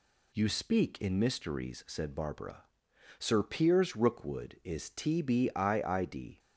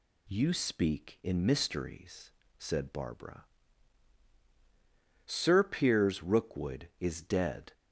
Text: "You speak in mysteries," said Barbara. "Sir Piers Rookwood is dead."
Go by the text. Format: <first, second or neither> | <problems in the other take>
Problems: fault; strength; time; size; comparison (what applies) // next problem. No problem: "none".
second | says "tbiid" for "dead"; at 4.8 s